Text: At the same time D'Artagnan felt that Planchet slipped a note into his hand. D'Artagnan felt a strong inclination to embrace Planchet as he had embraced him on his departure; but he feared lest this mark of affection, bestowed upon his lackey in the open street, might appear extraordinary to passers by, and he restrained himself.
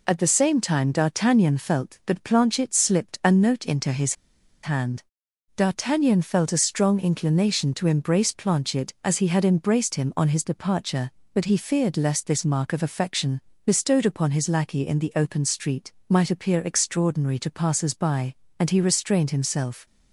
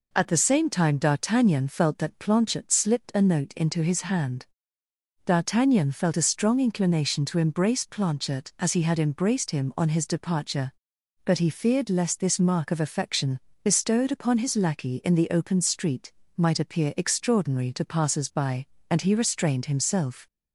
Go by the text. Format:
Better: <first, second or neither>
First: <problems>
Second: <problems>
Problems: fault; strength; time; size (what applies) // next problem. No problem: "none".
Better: second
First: pauses between "his" and "hand"; noticeable; at 4.1 s; 0.49 s long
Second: none